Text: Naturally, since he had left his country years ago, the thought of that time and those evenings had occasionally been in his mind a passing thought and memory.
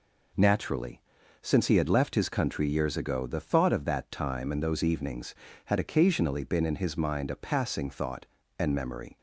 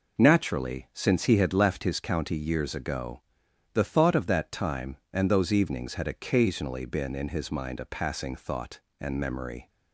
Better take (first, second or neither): first